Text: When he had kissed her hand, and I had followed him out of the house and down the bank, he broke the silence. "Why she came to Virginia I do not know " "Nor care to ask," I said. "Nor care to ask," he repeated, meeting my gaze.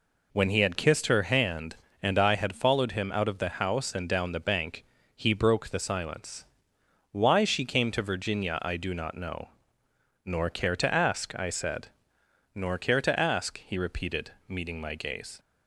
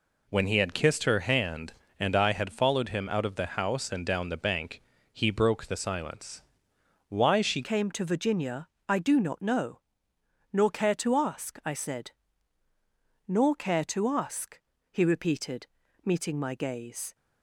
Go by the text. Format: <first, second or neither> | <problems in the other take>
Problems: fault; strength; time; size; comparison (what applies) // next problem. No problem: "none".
first | changes voice at "came"; from 7.6 s on; 9.5 s long // pauses between "Virginia" and "I"; slight; at 8.6 s; 0.20 s long